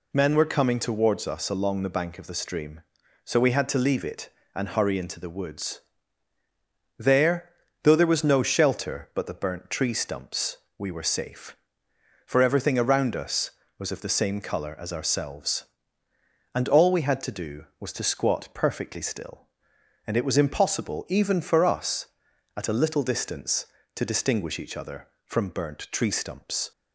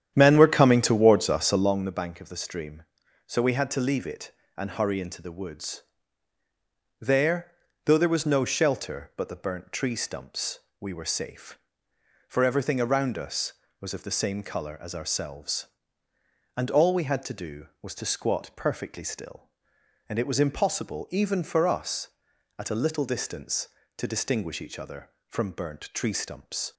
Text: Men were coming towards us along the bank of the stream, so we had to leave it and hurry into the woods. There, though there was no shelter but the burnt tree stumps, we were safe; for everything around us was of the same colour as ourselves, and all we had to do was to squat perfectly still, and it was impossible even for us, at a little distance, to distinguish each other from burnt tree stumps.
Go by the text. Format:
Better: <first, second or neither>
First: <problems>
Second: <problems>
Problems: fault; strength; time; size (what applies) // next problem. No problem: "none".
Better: first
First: none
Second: starts louder than the rest; strong; until 1.9 s; 10 dB